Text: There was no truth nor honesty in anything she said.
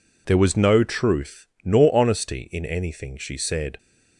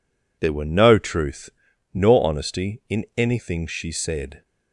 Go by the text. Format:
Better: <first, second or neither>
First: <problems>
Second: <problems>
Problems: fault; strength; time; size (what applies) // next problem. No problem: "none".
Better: first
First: pauses between "truth" and "nor"; slight; at 1.4 s; 0.18 s long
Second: says "were" for "was"; at 0.5 s // pauses between "truth" and "nor"; at 1.4 s; 0.44 s long